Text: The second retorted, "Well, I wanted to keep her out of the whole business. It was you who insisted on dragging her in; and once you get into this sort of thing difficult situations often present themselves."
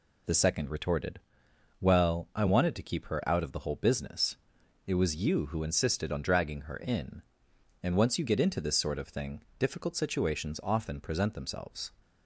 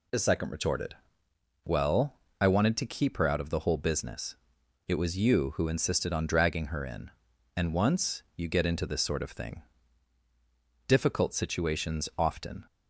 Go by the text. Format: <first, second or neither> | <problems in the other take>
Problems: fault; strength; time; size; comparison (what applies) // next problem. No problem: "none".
first | pauses between "thing" and "difficult"; strong; at 9.6 s; 1.2 s long; slight in the first // stops before "present themselves"; at 12.6 s